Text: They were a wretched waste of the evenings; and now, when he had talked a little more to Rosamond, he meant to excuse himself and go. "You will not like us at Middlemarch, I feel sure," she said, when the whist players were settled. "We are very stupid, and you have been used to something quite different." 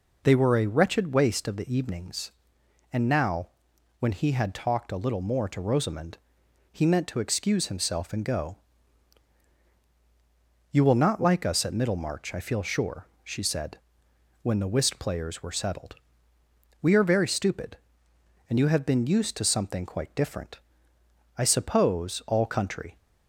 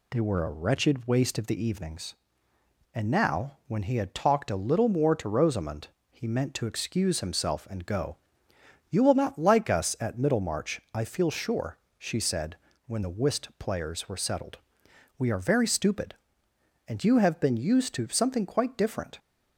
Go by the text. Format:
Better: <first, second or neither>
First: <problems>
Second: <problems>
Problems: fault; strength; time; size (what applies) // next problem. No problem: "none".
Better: second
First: goes on to say "I suppose all country"; from 21.3 s on; 1.6 s long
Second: none